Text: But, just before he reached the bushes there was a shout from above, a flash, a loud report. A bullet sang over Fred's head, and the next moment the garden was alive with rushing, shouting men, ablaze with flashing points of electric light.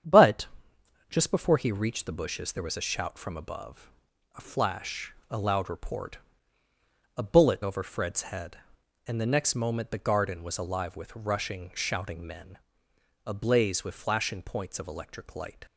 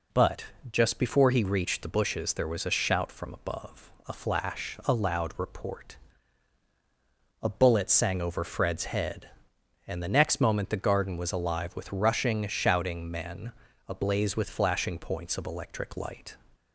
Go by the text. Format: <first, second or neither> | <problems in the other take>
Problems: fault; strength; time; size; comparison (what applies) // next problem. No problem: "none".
second | starts louder than the rest; strong; until 1.7 s; 8.5 dB // skips "sang"; at 7.6 s